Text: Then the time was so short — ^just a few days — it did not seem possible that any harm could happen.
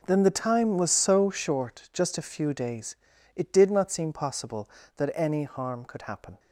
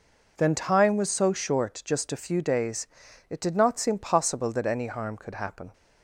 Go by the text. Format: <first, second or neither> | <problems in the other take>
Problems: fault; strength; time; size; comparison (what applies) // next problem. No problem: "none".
first | skips "the"; at 0.5 s